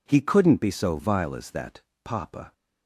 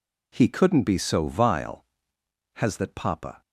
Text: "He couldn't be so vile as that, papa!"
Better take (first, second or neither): first